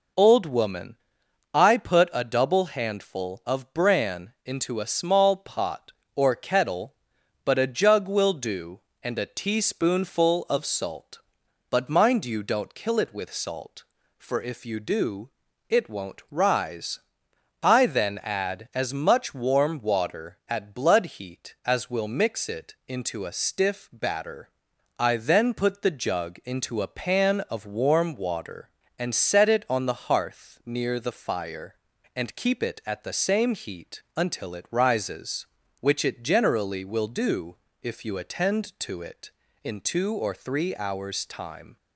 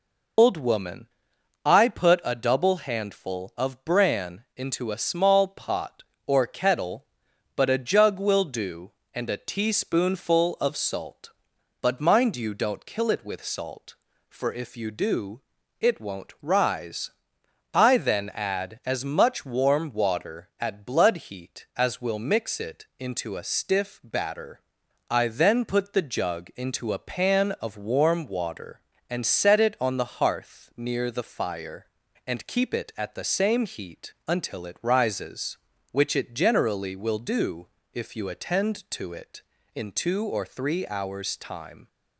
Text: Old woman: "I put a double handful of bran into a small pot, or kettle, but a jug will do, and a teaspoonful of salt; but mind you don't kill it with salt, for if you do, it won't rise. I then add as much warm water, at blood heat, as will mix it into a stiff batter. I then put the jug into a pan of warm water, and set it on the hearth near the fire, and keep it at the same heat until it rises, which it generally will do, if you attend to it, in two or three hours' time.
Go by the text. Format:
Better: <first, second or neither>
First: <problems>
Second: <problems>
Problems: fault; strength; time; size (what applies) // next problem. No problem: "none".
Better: first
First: none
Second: loses the start of "Old"; at 0.3 s; 105 ms